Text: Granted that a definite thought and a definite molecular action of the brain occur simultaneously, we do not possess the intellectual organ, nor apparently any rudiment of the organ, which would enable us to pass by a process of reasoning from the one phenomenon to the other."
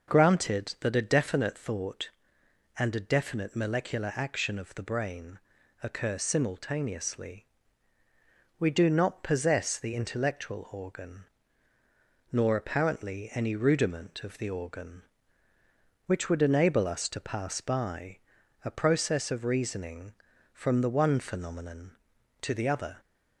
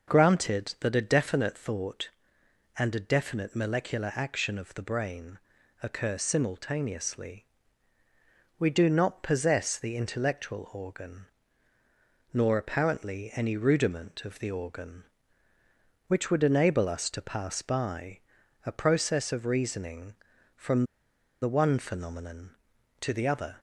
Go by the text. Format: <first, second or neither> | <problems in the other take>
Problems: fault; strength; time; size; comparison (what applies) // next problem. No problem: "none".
first | pauses between "brain" and "occur"; noticeable; at 5.3 s; 0.46 s long; noticeable in the first // pauses between "by" and "a"; noticeable; at 18.1 s; 0.46 s long; noticeable in the first // pauses between "from" and "the"; noticeable; at 20.8 s; 0.57 s long